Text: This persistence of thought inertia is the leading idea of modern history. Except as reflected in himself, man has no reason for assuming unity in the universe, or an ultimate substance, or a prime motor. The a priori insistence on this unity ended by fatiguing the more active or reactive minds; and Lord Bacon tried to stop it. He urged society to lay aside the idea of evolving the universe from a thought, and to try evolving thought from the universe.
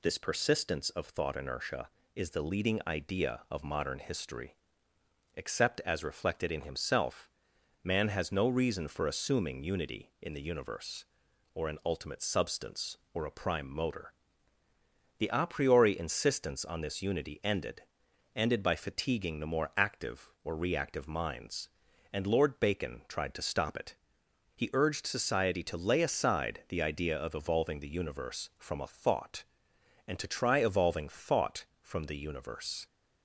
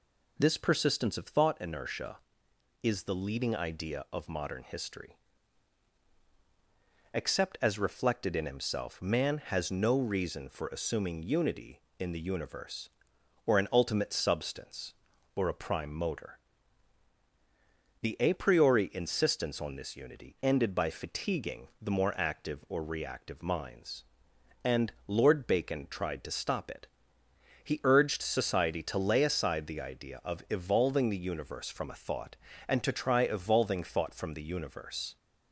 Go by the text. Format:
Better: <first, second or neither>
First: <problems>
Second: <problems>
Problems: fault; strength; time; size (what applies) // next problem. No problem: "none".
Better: second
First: says "ended" twice; at 18.3 s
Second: none